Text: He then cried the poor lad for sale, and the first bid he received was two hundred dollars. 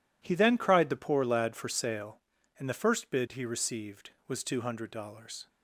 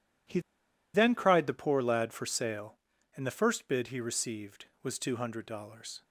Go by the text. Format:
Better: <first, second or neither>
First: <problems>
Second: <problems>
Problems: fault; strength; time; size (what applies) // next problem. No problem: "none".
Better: first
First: none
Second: pauses between "He" and "then"; noticeable; at 0.4 s; 0.53 s long